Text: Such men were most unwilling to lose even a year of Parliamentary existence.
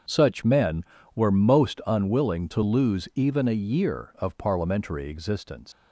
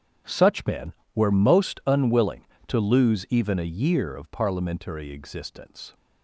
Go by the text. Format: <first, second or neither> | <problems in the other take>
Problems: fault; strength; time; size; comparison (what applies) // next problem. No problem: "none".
second | starts louder than the rest; strong; until 1.4 s; 7 dB; strong in the second // leaves "existence" unfinished; at 5.7 s; 80 ms